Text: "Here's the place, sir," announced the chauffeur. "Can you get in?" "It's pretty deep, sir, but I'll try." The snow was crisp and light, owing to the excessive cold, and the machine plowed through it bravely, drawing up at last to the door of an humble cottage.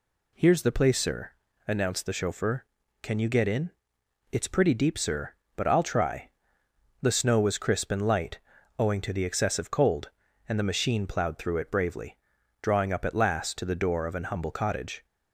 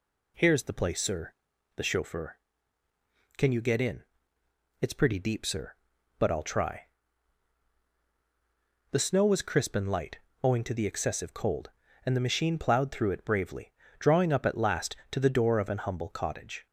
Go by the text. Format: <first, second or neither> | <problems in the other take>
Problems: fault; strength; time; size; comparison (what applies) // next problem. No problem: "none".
first | skips "announced"; at 1.5 s